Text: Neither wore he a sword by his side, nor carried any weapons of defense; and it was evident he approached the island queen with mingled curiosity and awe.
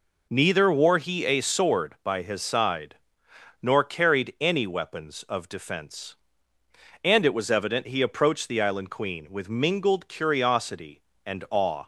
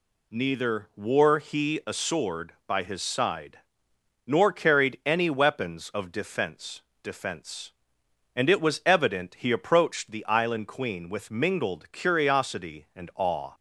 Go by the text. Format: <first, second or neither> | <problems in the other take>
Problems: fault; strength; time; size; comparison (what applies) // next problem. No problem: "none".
first | says "defense" twice; at 7.0 s